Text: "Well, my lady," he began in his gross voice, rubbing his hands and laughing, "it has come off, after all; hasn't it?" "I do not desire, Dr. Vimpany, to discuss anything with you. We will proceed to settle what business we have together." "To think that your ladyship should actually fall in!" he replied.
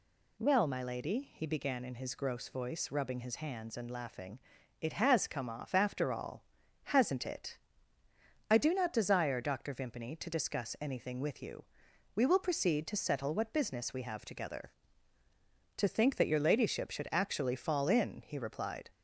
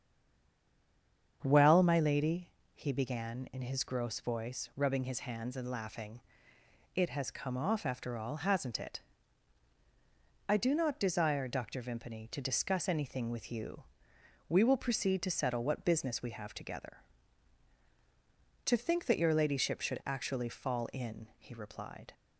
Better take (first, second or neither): first